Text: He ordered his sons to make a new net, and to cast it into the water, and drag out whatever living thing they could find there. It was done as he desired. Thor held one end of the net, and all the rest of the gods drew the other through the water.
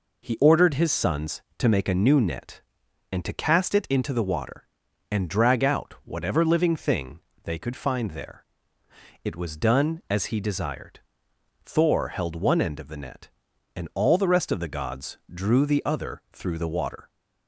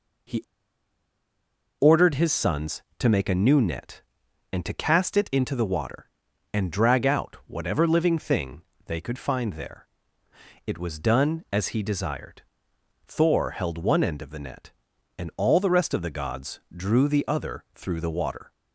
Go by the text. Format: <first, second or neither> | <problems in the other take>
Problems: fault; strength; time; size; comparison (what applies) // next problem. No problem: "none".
first | pauses between "He" and "ordered"; strong; at 0.4 s; 1.3 s long // pauses between "thing" and "they"; slight; at 8.6 s; 0.24 s long; slight in the first